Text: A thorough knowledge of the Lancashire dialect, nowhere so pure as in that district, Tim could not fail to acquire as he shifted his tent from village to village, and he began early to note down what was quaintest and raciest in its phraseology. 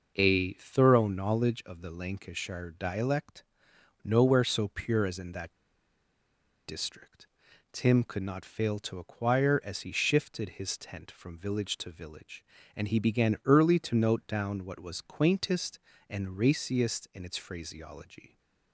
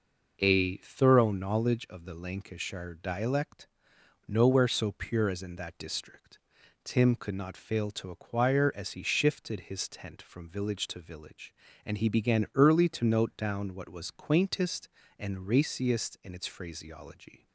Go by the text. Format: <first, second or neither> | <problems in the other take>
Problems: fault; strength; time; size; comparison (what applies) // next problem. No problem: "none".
second | pauses between "that" and "district"; at 5.5 s; 1.1 s long